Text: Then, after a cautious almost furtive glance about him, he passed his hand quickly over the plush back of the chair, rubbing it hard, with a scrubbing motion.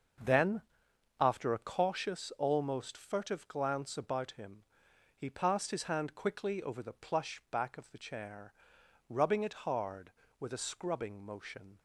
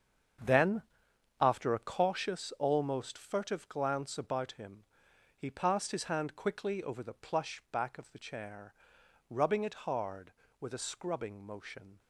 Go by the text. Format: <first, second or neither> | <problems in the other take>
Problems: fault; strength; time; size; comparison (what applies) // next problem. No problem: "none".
first | gets quieter; strong; throughout; 10.5 dB // starts louder than the rest; strong; until 2.0 s; 7 dB; noticeable in the first